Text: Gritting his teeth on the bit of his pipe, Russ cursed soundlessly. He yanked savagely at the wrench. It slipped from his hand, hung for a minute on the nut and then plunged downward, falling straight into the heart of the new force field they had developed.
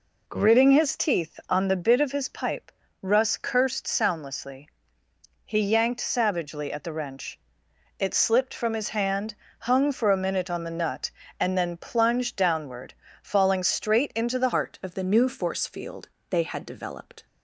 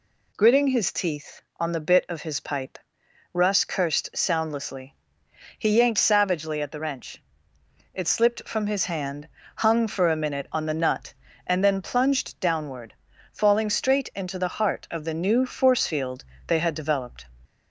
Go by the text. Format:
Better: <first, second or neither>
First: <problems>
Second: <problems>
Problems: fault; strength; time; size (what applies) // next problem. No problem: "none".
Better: second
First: changes voice at "heart"; from 14.5 s on; 2.7 s long // pauses between "field" and "they"; slight; at 16.0 s; 0.24 s long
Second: pauses between "field" and "they"; slight; at 16.2 s; 0.24 s long